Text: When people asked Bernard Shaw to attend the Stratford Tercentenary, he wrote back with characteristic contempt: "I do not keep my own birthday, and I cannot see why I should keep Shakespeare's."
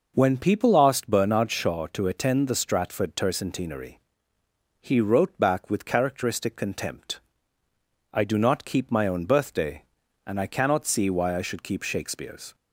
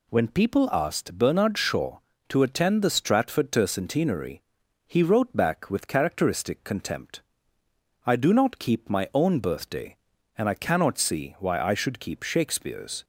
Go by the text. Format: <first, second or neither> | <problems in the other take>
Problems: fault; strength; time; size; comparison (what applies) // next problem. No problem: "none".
neither | none